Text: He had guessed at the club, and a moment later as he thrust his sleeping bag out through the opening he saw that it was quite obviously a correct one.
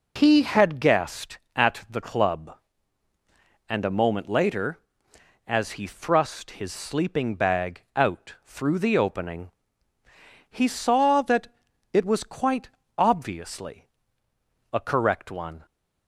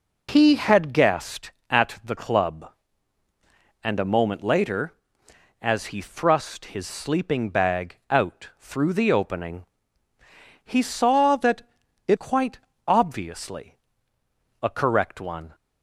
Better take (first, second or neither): first